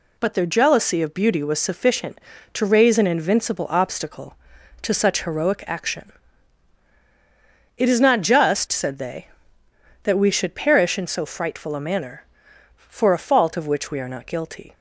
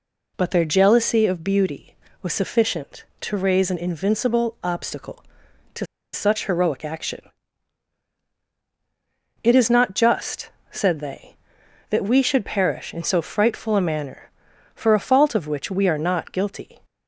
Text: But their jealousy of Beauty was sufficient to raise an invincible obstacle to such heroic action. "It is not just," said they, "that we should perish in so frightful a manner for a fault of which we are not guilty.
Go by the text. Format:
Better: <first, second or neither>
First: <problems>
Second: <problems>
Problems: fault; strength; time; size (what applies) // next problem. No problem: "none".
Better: first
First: none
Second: pauses between "to" and "such"; slight; at 5.8 s; 0.27 s long